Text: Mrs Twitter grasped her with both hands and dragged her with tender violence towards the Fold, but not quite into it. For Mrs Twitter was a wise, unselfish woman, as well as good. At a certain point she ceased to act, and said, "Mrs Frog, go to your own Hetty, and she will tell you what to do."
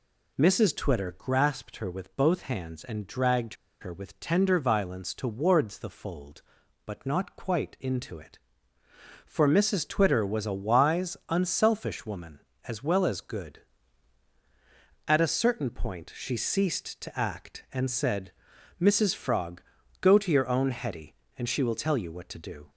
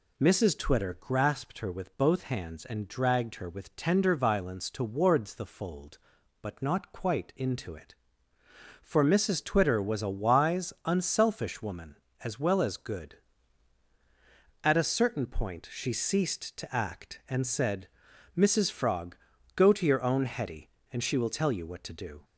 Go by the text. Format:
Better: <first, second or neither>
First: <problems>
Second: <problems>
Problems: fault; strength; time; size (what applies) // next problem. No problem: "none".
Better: second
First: pauses between "dragged" and "her"; slight; at 3.5 s; 0.26 s long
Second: none